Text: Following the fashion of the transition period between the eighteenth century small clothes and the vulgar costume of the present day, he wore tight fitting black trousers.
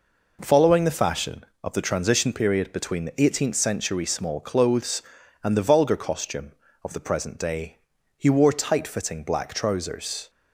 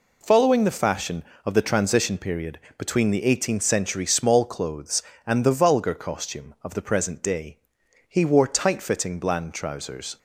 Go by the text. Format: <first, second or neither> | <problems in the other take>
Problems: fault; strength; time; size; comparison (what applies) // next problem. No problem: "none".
first | pauses between "period" and "between"; slight; at 2.5 s; 0.18 s long // says "bland" for "black"; at 9.1 s